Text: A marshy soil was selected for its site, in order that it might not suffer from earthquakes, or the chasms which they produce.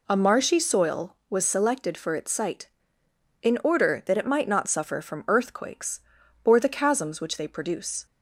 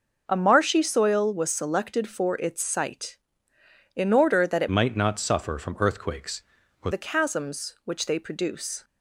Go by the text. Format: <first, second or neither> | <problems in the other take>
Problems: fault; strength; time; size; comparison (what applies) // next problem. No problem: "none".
first | changes voice from "might" to "or"; from 4.7 to 6.8 s; 2.1 s long